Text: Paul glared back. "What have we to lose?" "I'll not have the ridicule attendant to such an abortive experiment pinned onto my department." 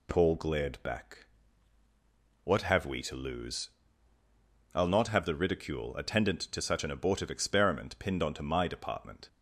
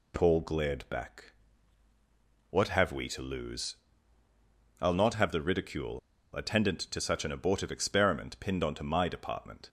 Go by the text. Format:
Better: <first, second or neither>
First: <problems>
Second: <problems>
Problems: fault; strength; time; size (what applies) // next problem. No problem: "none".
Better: first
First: none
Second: pauses between "ridicule" and "attendant"; at 5.9 s; 0.36 s long